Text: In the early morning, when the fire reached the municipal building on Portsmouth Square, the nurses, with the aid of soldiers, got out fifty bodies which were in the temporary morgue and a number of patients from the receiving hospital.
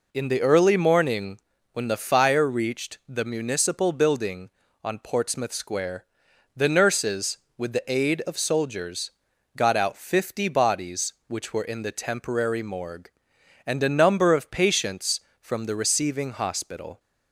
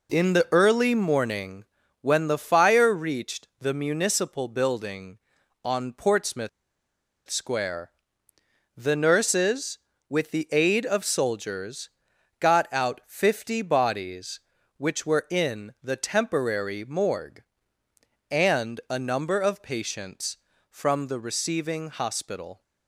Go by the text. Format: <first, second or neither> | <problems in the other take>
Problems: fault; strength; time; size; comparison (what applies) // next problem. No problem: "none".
first | pauses between "Portsmouth" and "Square"; noticeable; at 6.4 s; 0.79 s long